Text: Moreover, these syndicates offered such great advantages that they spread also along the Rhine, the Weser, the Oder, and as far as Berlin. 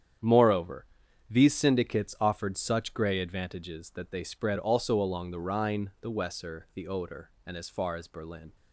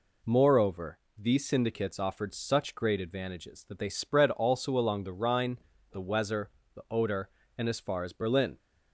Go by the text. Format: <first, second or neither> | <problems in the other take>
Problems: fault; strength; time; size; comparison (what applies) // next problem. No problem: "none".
second | starts louder than the rest; strong; until 1.6 s; 8.5 dB // says "grey" for "great"; at 2.9 s